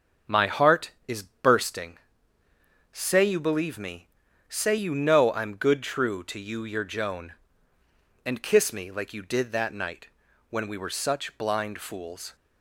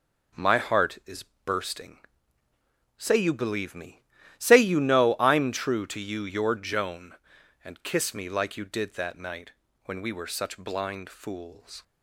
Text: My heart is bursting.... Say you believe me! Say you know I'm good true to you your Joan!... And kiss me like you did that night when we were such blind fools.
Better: first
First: pauses between "night" and "when"; at 10.0 s; 0.42 s long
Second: pauses between "is" and "bursting"; slight; at 1.2 s; 0.20 s long // skips "good"; at 5.5 s // pauses between "night" and "when"; at 9.5 s; 0.36 s long

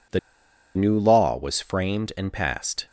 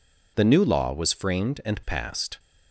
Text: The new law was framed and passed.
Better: second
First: pauses between "The" and "new"; noticeable; at 0.1 s; 0.56 s long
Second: none

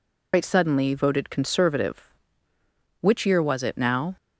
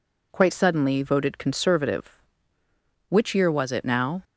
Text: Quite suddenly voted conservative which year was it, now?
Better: second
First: loses the start of "Quite"; at 0.3 s; 110 ms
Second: none

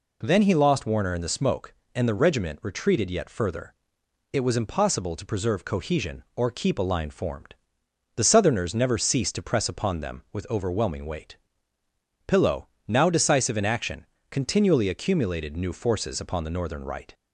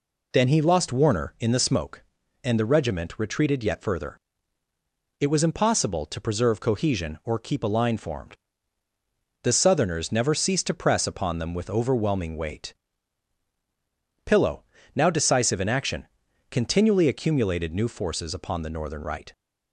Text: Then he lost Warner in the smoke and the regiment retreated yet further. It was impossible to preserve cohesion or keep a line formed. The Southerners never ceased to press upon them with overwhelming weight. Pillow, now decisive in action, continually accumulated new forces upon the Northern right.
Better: neither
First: none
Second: none

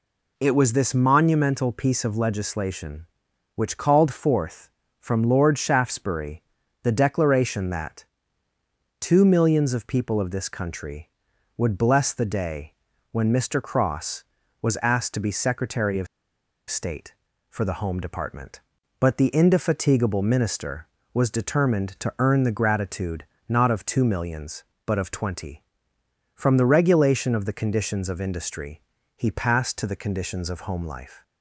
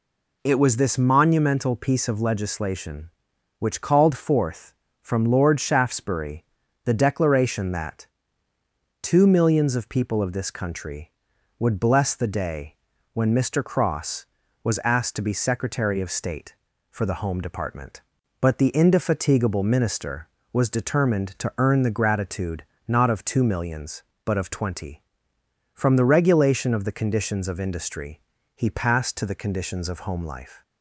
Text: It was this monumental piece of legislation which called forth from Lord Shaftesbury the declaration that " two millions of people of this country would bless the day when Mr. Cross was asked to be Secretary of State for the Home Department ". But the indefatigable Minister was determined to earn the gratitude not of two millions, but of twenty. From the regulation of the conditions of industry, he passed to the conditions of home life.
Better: second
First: pauses between "Shaftesbury" and "the"; at 6.4 s; 0.40 s long // pauses between "day" and "when"; at 12.7 s; 0.38 s long // pauses between "of" and "State"; noticeable; at 16.0 s; 0.64 s long // pauses between "gratitude" and "not"; slight; at 23.2 s; 0.20 s long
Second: pauses between "Shaftesbury" and "the"; at 6.4 s; 0.40 s long // pauses between "day" and "when"; at 12.7 s; 0.38 s long // pauses between "gratitude" and "not"; slight; at 22.6 s; 0.20 s long

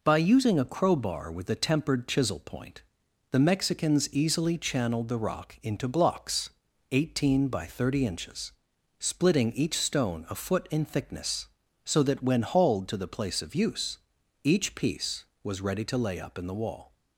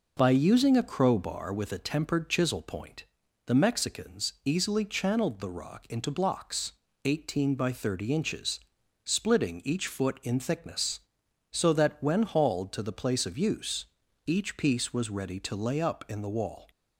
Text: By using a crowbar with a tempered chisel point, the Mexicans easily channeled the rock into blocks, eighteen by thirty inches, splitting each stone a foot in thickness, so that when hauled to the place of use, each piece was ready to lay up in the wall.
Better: first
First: none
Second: skips "stone a"; at 9.8 s

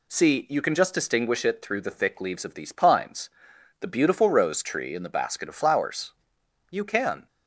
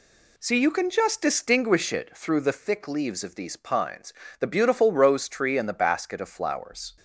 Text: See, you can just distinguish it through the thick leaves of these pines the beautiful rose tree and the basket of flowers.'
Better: second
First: pauses between "pines" and "the"; noticeable; at 3.2 s; 0.52 s long // goes on to say "You can"; from 6.7 s on; 0.56 s long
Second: pauses between "pines" and "the"; slight; at 4.1 s; 0.26 s long

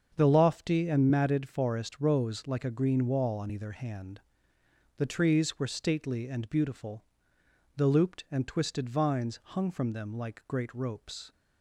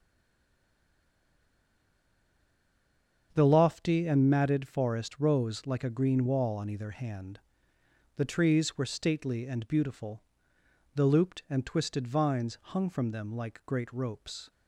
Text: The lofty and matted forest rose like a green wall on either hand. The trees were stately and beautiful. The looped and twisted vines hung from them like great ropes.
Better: first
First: starts louder than the rest; strong; until 1.1 s; 7 dB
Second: stays silent before the first word; strong; until 3.3 s; 3.3 s long // starts louder than the rest; strong; until 4.3 s; 7 dB

